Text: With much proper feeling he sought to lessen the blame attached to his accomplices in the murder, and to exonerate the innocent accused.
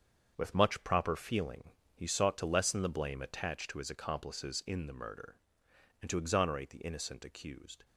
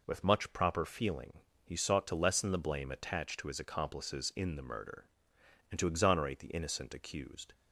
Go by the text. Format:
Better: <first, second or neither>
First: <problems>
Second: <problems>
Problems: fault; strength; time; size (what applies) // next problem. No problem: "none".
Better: second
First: gets quieter; strong; throughout; 9.5 dB // pauses between "feeling" and "he"; slight; at 1.7 s; 0.24 s long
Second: pauses between "feeling" and "he"; slight; at 1.4 s; 0.24 s long